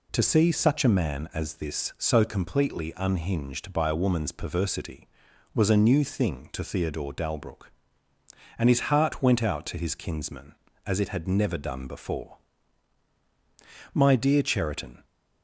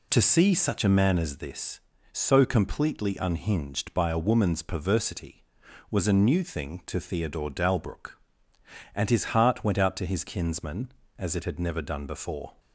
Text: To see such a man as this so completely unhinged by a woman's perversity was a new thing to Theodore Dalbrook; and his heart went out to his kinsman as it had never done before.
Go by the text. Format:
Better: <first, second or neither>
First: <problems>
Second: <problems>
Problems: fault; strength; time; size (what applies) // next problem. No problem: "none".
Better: second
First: goes on to say "My dear Cheriton"; noticeable; from 13.9 s on; 1.1 s long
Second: none